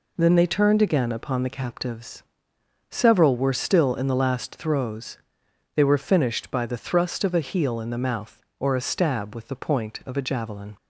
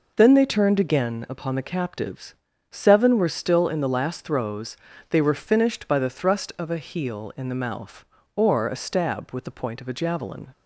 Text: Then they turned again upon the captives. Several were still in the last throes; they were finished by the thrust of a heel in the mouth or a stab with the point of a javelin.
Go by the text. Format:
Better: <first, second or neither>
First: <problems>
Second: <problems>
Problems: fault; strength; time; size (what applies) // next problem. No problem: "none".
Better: first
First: none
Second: says "Seven" for "Several"; at 2.7 s